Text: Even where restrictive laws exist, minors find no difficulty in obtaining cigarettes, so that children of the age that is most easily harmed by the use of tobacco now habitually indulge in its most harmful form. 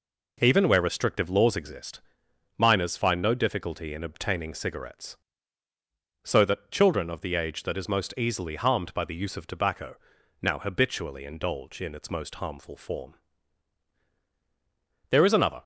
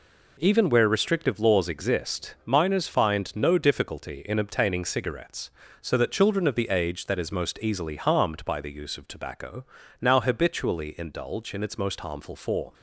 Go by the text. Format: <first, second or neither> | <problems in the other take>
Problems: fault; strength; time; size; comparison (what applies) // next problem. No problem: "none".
second | pauses between "tobacco" and "now"; at 9.9 s; 0.44 s long; slight in the second // goes on to say "There is another"; from 15.1 s on; 0.52 s long